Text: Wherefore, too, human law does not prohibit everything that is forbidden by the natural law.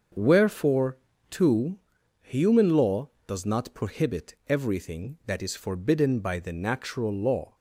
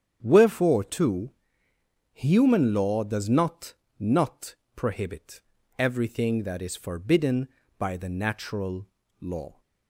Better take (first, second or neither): first